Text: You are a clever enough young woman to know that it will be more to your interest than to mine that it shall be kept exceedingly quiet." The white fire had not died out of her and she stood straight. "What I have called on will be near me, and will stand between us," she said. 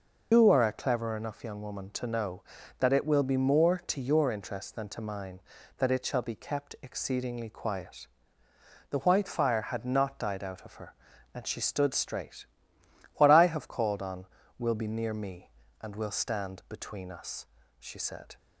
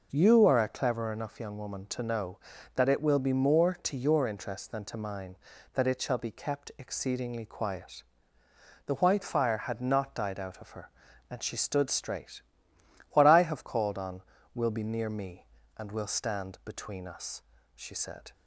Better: second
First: loses the start of "You"; at 0.3 s; 160 ms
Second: none

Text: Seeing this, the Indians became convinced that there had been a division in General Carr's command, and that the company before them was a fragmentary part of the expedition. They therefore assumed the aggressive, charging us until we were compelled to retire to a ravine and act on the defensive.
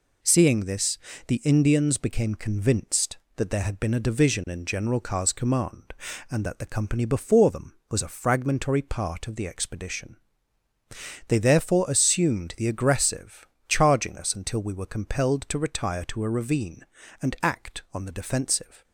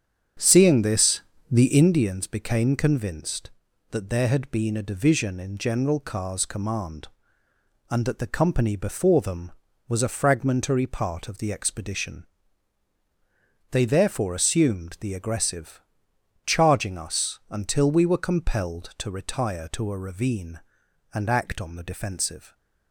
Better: first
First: none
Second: starts louder than the rest; strong; until 1.8 s; 7.5 dB

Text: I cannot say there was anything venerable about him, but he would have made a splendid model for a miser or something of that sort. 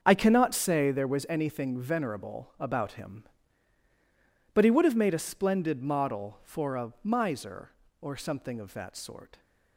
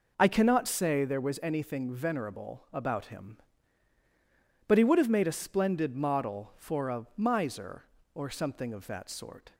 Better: second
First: gets quieter; strong; throughout; 11.5 dB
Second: none

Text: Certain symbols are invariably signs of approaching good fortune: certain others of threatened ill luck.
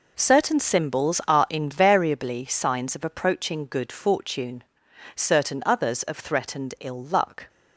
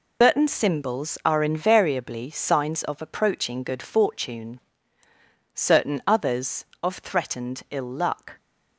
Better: first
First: none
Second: loses the start of "Certain"; at 0.2 s; 155 ms

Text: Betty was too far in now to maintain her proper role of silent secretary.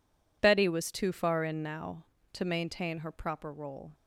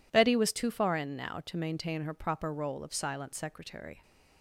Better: second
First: stops before "of silent secretary"; at 3.9 s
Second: none

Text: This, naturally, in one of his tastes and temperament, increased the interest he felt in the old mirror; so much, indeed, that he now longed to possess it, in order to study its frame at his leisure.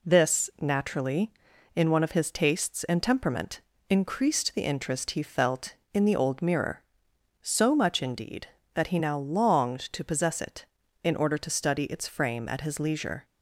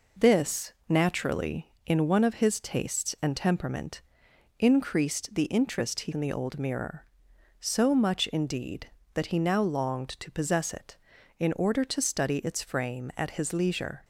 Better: first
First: none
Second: skips "felt"; at 6.1 s

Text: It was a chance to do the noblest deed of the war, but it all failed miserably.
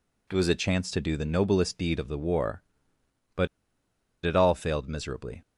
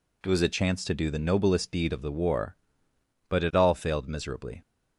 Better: second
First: pauses between "but" and "it"; noticeable; at 3.4 s; 0.75 s long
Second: none

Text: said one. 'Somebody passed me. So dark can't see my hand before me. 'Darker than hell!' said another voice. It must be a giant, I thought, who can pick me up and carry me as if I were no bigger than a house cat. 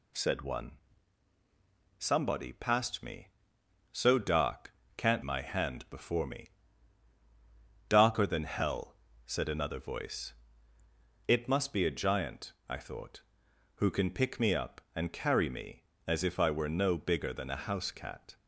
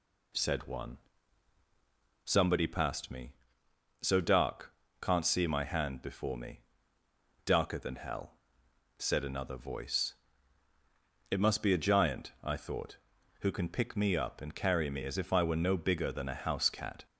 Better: second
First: pauses between "dark" and "can't"; slight; at 4.7 s; 0.24 s long // skips "see"; at 5.2 s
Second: pauses between "dark" and "can't"; slight; at 4.7 s; 0.26 s long

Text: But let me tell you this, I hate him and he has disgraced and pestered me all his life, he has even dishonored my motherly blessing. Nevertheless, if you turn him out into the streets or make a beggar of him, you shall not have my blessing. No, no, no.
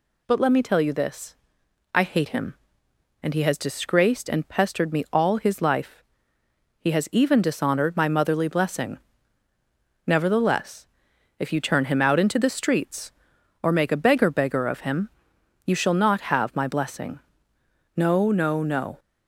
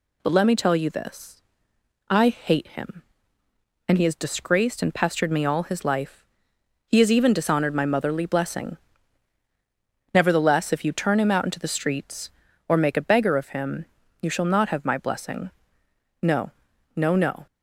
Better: second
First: says "beggar" twice; at 14.2 s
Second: none

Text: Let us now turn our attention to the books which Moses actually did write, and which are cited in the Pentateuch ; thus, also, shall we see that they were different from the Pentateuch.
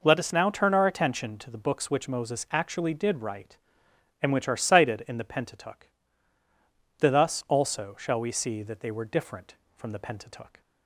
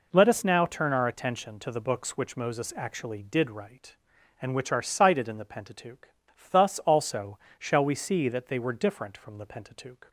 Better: neither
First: none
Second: none

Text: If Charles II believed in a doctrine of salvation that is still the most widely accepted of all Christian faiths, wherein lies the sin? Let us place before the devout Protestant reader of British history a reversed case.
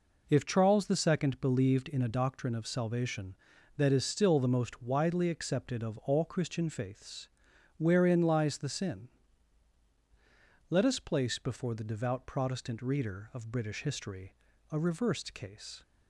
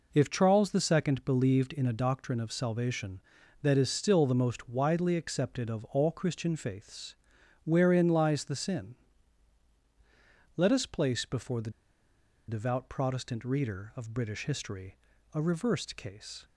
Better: first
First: pauses between "history" and "a"; slight; at 14.3 s; 0.36 s long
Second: pauses between "the" and "devout"; noticeable; at 11.7 s; 0.77 s long // pauses between "history" and "a"; slight; at 14.9 s; 0.36 s long

